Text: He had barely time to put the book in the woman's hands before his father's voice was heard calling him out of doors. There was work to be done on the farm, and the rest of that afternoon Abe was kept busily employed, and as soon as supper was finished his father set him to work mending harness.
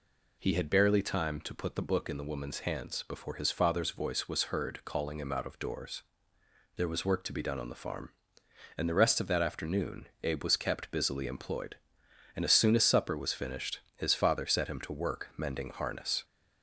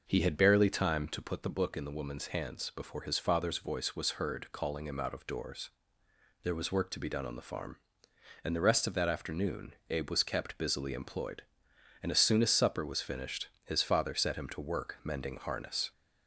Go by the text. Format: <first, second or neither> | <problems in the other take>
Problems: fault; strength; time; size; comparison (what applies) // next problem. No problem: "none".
first | starts louder than the rest; noticeable; until 1.3 s; 6 dB // pauses between "afternoon" and "Abe"; slight; at 9.7 s; 0.16 s long; slight in the first